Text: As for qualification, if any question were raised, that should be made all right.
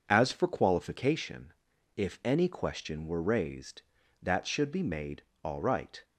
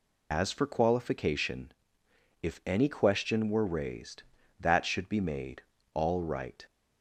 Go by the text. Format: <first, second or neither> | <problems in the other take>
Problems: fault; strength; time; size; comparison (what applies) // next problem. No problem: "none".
first | loses the start of "As"; at 0.3 s; 105 ms // pauses between "made" and "all"; slight; at 5.6 s; 0.32 s long; slight in the first